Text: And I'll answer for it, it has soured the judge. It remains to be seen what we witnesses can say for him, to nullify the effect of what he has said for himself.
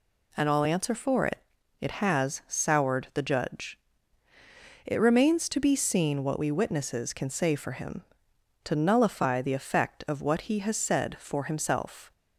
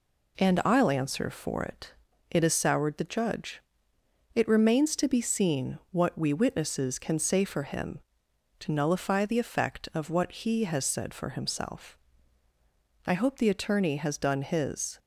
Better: first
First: none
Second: goes on to say "I hope the attorney has done his"; strong; from 13.0 s on; 1.9 s long

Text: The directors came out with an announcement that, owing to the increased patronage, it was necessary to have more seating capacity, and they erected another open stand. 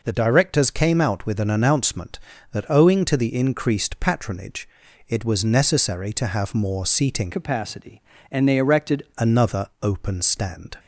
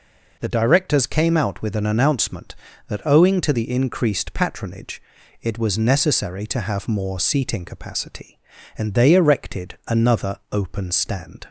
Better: second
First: changes voice from "capacity" to "erected"; from 7.3 to 9.0 s; 1.7 s long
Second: none

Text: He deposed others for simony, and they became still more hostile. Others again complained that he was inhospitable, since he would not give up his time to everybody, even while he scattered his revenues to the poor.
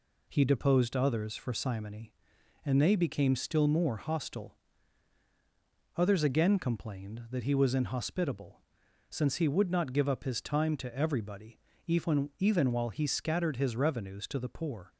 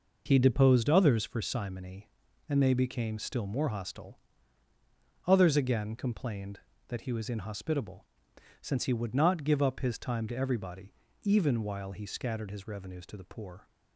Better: second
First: says "even" twice; at 12.3 s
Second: none

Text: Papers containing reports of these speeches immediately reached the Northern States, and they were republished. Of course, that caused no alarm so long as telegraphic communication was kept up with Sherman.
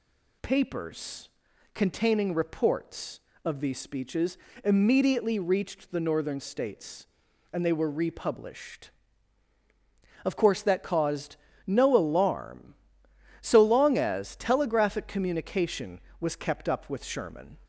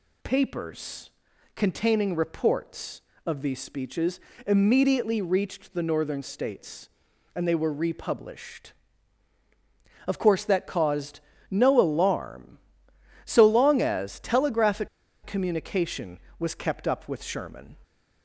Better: first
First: pauses between "Papers" and "containing"; at 1.2 s; 0.44 s long // pauses between "speeches" and "immediately"; slight; at 4.3 s; 0.28 s long // pauses between "caused" and "no"; slight; at 11.3 s; 0.30 s long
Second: pauses between "Papers" and "containing"; at 1.1 s; 0.44 s long // pauses between "speeches" and "immediately"; slight; at 4.1 s; 0.28 s long // pauses between "caused" and "no"; slight; at 11.2 s; 0.30 s long // pauses between "telegraphic" and "communication"; at 14.8 s; 0.37 s long

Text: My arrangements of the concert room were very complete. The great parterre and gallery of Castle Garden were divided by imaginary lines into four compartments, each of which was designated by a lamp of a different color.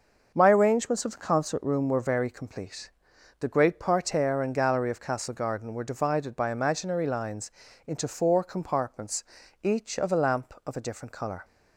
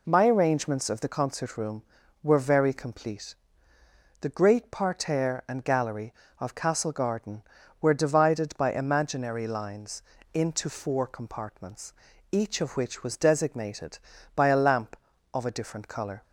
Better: second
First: starts louder than the rest; noticeable; until 1.3 s; 6 dB // pauses between "lines" and "into"; slight; at 7.5 s; 0.36 s long // skips "which was designated by"; at 10.1 s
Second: pauses between "lines" and "into"; slight; at 10.0 s; 0.32 s long

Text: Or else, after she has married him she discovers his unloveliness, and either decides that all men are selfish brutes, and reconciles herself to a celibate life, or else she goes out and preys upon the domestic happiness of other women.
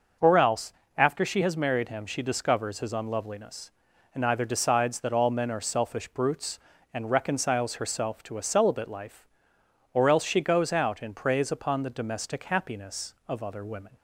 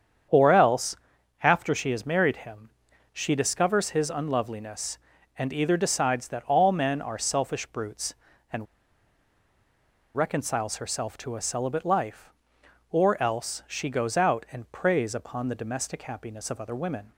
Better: first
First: starts louder than the rest; noticeable; until 1.4 s; 6 dB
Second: starts louder than the rest; strong; until 1.7 s; 8 dB // pauses between "him" and "she"; at 2.6 s; 0.42 s long // pauses between "and" and "reconciles"; strong; at 8.6 s; 1.4 s long

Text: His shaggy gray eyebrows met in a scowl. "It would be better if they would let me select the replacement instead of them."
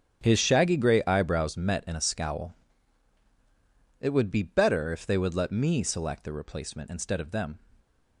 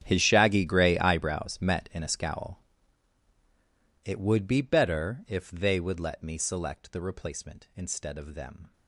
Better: first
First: starts louder than the rest; strong; until 1.2 s; 9 dB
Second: gets quieter; strong; throughout; 18.5 dB // starts louder than the rest; strong; until 1.0 s; 9.5 dB

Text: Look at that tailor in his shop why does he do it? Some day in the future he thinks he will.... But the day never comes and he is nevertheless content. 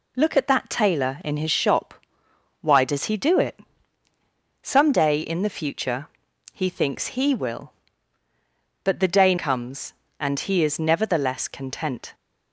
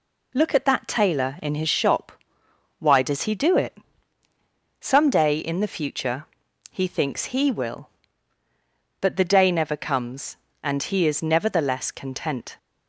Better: second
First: pauses between "shop" and "why"; noticeable; at 1.9 s; 0.68 s long // pauses between "future" and "he"; at 6.0 s; 0.44 s long // skips "never"; at 9.3 s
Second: pauses between "shop" and "why"; noticeable; at 2.1 s; 0.68 s long // pauses between "future" and "he"; at 6.2 s; 0.44 s long

